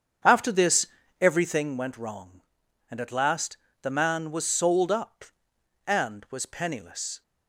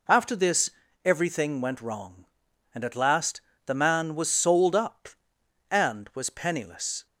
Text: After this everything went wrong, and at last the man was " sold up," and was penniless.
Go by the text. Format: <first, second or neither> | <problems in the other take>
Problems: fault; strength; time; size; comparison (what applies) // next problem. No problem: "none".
second | starts louder than the rest; strong; until 1.7 s; 7.5 dB // pauses between "this" and "everything"; slight; at 0.8 s; 0.34 s long; slight in the second // pauses between "last" and "the"; slight; at 3.5 s; 0.26 s long; slight in the second